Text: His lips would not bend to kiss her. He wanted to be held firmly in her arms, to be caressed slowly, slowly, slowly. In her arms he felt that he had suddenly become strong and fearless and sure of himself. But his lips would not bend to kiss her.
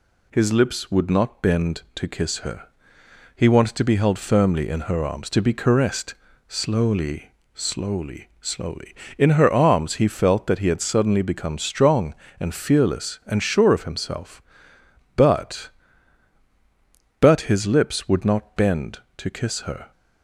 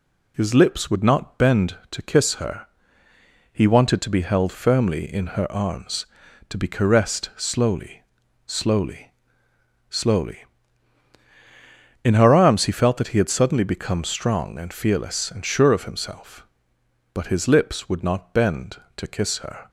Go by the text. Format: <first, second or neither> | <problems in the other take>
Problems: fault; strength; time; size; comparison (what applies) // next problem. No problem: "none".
second | pauses between "caressed" and "slowly"; slight; at 6.1 s; 0.32 s long // says "But" twice; at 17.1 s